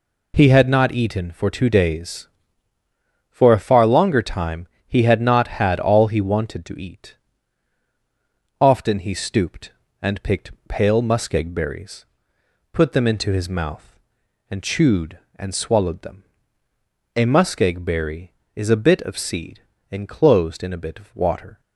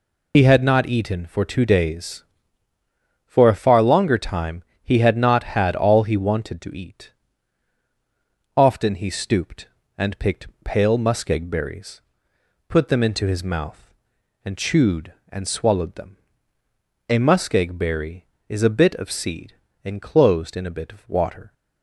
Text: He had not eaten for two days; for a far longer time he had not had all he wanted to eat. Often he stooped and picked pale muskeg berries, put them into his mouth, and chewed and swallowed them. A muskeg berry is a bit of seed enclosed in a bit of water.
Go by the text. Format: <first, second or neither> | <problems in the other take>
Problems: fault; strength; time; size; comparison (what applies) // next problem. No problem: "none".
first | loses the start of "He"; at 0.3 s; 65 ms // pauses between "time" and "he"; slight; at 4.6 s; 0.22 s long; slight in the first // pauses between "picked" and "pale"; slight; at 10.4 s; 0.18 s long; slight in the first // pauses between "seed" and "enclosed"; slight; at 19.5 s; 0.32 s long; slight in the first